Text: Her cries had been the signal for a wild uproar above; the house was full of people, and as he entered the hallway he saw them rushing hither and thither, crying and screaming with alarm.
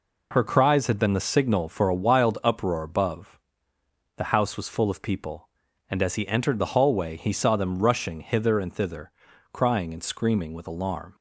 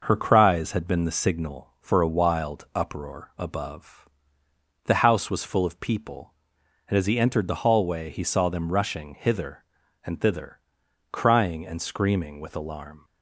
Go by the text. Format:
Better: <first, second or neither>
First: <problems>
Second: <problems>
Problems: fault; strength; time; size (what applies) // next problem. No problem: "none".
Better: neither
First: none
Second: none